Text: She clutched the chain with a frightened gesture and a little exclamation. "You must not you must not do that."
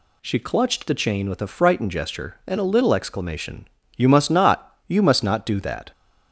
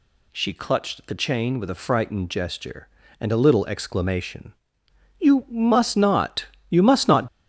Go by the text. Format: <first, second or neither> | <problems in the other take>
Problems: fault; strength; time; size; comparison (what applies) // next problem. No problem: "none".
first | pauses between "not" and "you"; slight; at 6.4 s; 0.26 s long // stops before "do that"; at 7.2 s